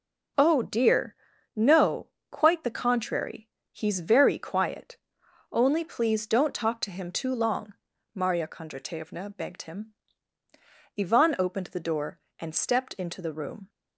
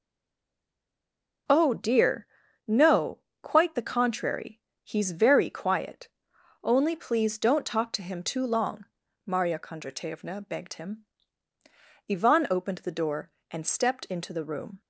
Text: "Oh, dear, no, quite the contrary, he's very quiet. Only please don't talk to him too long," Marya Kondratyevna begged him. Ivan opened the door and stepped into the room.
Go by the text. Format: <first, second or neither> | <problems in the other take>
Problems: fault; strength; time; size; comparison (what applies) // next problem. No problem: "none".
first | stays silent before the first word; noticeable; until 1.4 s; 1.4 s long